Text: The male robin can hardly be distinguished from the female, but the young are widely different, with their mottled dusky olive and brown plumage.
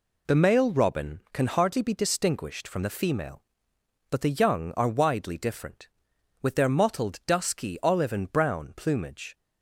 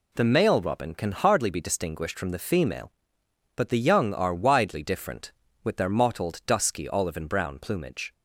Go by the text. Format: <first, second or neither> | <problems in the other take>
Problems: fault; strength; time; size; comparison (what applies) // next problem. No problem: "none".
neither | none